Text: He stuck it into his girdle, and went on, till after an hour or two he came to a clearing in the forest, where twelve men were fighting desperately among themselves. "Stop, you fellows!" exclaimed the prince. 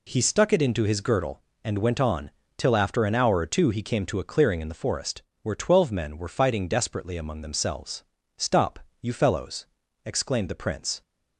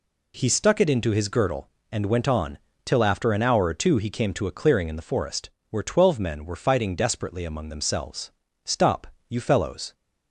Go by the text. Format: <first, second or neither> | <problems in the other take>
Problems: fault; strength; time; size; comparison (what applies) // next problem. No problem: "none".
first | stops before "exclaimed the prince"; at 9.9 s